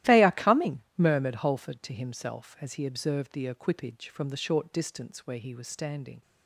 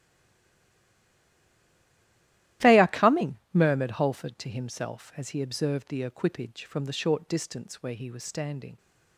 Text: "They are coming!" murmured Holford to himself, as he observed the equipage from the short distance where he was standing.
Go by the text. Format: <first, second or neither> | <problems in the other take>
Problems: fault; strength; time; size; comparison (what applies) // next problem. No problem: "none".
first | stays silent before the first word; strong; until 2.6 s; 2.6 s long // starts louder than the rest; strong; until 3.7 s; 14.5 dB; strong in the first